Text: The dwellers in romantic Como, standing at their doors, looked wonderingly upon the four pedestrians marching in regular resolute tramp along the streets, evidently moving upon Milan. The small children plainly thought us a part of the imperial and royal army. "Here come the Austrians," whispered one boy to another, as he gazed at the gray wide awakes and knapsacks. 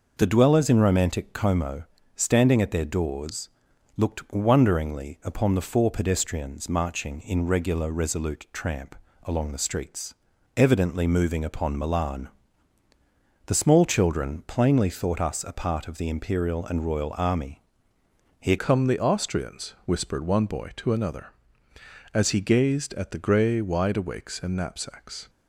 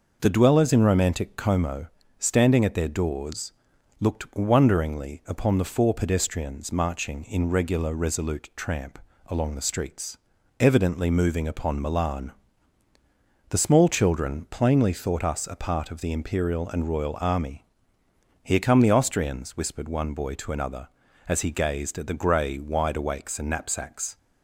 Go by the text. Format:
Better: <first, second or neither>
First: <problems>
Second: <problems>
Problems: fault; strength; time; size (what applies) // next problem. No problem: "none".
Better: second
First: pauses between "tramp" and "along"; slight; at 8.9 s; 0.30 s long // changes voice at "come"; from 18.5 s on; 6.7 s long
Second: pauses between "tramp" and "along"; slight; at 8.9 s; 0.30 s long